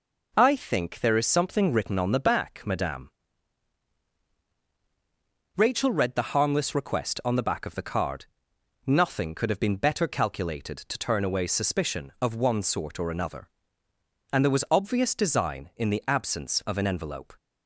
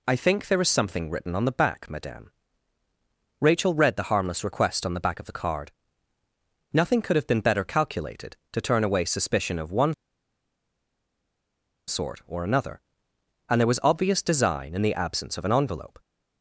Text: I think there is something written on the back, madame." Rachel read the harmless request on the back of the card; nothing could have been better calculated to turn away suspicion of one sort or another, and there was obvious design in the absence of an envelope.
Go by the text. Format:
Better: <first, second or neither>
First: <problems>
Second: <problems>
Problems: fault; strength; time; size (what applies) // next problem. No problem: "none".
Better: first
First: none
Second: pauses between "one" and "sort"; strong; at 9.9 s; 1.9 s long